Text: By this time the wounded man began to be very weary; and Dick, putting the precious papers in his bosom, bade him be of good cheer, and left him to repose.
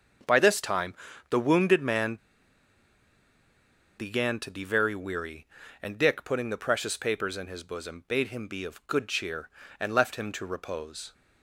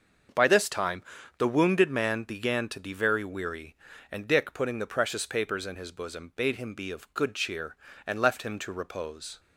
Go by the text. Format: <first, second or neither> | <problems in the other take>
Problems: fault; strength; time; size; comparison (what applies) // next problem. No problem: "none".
second | starts louder than the rest; until 1.6 s; 6.5 dB; also in the second // pauses between "time" and "the"; slight; at 0.9 s; 0.36 s long; slight in the second // pauses between "man" and "began"; strong; at 2.1 s; 1.8 s long